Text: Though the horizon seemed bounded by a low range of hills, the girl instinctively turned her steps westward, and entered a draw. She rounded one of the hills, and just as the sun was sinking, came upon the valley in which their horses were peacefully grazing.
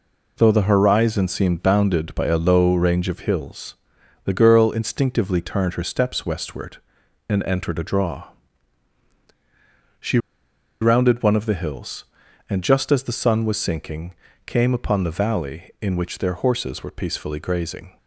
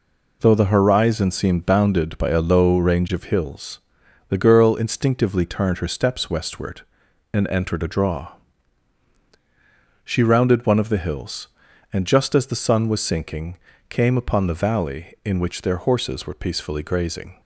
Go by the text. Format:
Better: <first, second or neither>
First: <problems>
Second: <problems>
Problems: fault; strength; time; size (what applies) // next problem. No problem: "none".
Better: second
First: pauses between "She" and "rounded"; noticeable; at 10.1 s; 0.63 s long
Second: none